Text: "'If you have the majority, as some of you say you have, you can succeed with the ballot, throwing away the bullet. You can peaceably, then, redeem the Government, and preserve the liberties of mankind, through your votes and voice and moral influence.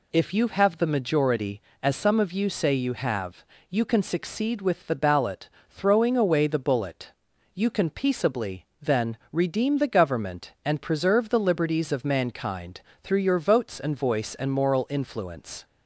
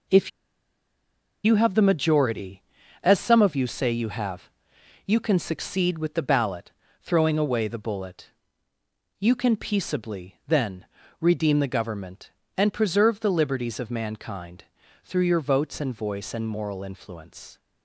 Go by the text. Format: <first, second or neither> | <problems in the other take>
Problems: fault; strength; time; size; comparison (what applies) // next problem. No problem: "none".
first | pauses between "If" and "you"; at 0.3 s; 1.1 s long